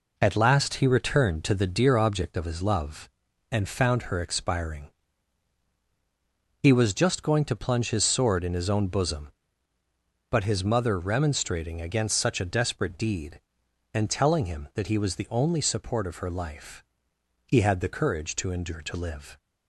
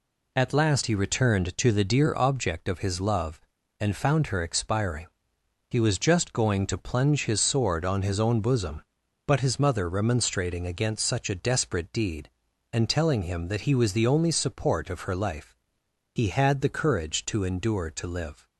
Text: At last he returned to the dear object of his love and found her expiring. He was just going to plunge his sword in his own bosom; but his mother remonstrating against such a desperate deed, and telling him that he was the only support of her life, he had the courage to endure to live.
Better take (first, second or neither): first